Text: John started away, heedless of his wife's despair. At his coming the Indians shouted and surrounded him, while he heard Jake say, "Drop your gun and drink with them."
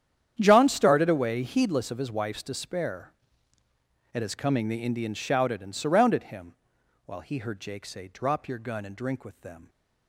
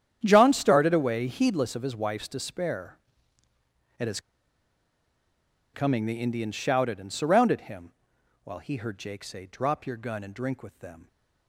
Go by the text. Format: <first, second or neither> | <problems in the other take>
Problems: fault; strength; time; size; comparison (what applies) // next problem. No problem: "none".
first | starts louder than the rest; strong; until 1.2 s; 9.5 dB; strong in the first // pauses between "his" and "coming"; strong; at 4.1 s; 1.5 s long